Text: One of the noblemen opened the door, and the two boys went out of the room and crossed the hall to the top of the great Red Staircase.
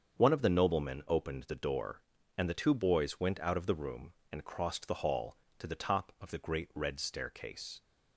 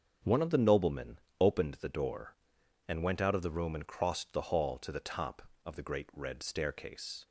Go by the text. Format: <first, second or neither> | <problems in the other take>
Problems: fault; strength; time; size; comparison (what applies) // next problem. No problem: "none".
first | starts louder than the rest; until 1.4 s; 7 dB; strong in the first // pauses between "noblemen" and "opened"; slight; at 1.1 s; 0.22 s long // skips "the two boys"; at 3.0 s